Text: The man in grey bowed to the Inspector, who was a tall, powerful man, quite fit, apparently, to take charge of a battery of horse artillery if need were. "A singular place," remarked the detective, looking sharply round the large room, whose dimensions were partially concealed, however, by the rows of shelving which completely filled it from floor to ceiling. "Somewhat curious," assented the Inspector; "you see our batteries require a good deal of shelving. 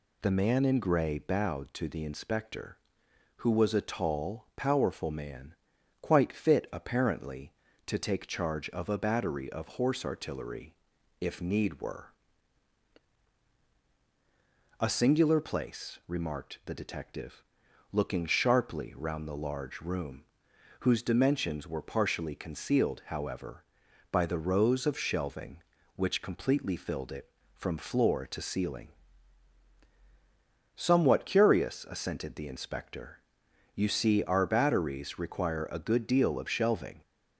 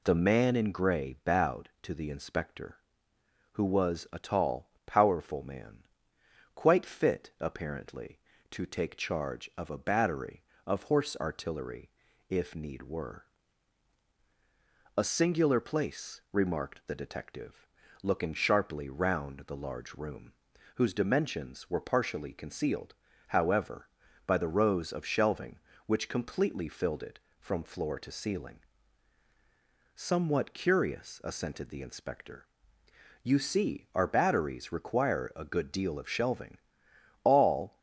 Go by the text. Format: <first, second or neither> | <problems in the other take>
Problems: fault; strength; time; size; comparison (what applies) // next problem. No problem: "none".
first | pauses between "artillery" and "if"; at 11.8 s; 0.40 s long; noticeable in the first // goes on to say "All"; from 37.2 s on; 0.54 s long